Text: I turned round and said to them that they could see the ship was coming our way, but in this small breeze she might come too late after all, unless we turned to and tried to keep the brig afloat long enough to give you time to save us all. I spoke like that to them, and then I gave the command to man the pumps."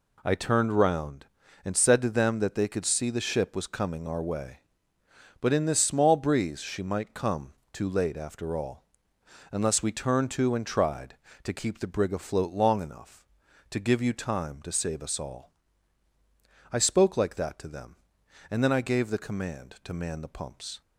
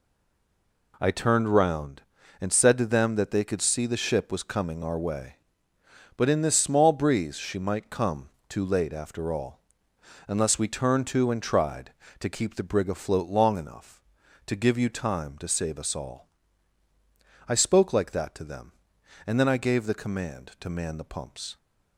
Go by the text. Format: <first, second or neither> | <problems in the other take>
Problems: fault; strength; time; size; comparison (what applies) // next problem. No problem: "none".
first | stays silent before the first word; slight; until 0.9 s; 0.9 s long // pauses between "come" and "too"; slight; at 8.2 s; 0.20 s long; slight in the first